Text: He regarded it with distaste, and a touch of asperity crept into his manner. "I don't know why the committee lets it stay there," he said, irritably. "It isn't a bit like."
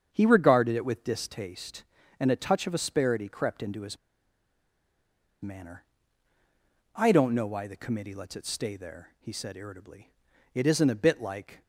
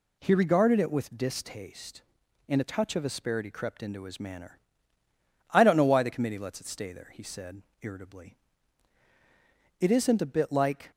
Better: second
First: starts louder than the rest; strong; until 1.1 s; 7.5 dB // pauses between "his" and "manner"; strong; at 3.9 s; 1.4 s long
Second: none

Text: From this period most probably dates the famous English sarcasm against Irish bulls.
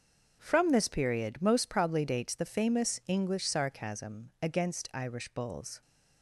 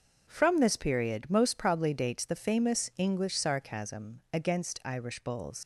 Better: first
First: starts louder than the rest; until 1.4 s; 6.5 dB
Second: starts louder than the rest; until 1.2 s; 6.5 dB // leaves "bulls" unfinished; at 5.6 s; 75 ms

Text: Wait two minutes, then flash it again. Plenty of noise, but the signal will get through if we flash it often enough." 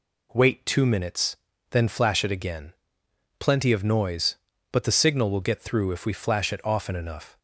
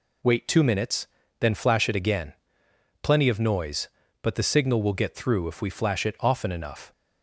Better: neither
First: none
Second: none

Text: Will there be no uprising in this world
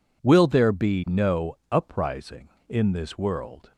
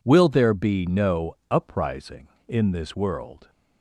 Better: neither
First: none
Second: none

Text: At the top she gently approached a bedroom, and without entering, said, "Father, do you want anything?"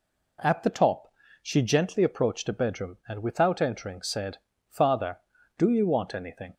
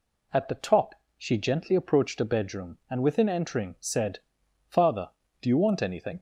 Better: first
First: pauses between "top" and "she"; slight; at 1.1 s; 0.30 s long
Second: pauses between "top" and "she"; slight; at 0.9 s; 0.24 s long // says "within" for "without"; at 3.0 s

